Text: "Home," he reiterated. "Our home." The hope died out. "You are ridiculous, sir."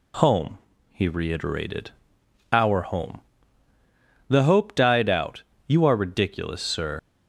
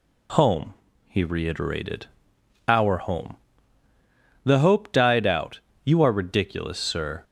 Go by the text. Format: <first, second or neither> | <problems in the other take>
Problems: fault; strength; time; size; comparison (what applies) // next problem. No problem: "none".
second | leaves "sir" unfinished; at 6.9 s; 75 ms